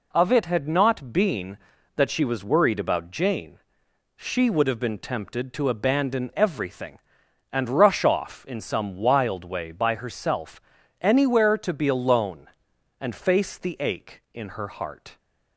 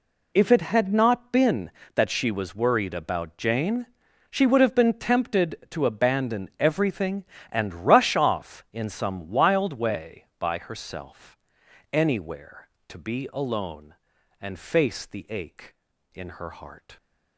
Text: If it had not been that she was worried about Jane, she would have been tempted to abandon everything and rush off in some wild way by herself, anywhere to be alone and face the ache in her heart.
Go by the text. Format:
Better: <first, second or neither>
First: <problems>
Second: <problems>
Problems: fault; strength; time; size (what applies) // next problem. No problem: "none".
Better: second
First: says "Of" for "If"; at 0.1 s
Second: none